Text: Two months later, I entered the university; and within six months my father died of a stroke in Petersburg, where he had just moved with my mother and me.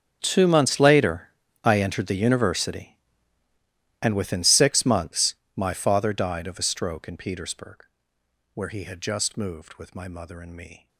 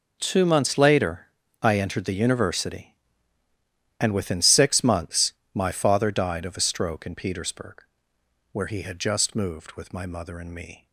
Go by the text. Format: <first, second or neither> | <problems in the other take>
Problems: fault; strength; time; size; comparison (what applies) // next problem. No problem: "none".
second | gets quieter; strong; throughout; 20 dB // pauses between "months" and "my"; slight; at 5.3 s; 0.22 s long; slight in the second